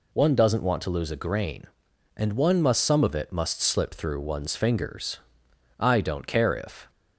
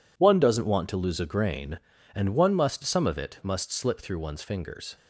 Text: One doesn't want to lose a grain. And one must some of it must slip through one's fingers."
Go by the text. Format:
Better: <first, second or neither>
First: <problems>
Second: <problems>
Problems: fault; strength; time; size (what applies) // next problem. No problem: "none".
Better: second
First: goes on to say "I don't care if"; noticeable; from 5.7 s on; 1.1 s long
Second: none